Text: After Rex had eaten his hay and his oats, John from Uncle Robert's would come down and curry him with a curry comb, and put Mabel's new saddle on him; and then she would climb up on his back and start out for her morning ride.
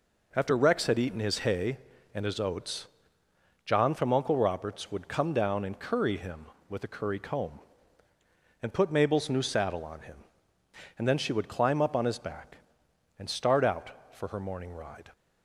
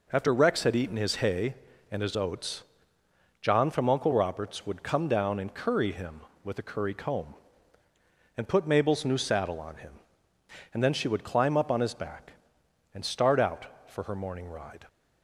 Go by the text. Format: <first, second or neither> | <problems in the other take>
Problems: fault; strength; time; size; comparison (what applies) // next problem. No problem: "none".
neither | none